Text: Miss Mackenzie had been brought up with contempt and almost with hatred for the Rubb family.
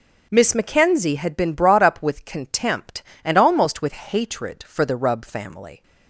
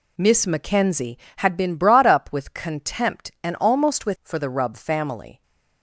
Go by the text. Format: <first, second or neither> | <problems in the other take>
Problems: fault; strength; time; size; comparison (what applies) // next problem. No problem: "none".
first | skips "hatred"; at 4.1 s